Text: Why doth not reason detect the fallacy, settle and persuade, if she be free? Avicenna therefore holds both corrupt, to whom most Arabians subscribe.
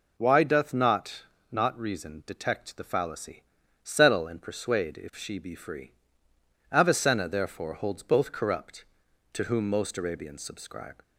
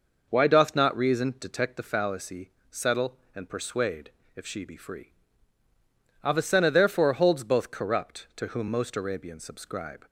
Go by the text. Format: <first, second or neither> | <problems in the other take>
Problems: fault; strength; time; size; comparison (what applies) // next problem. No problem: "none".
second | says "not" twice; at 1.5 s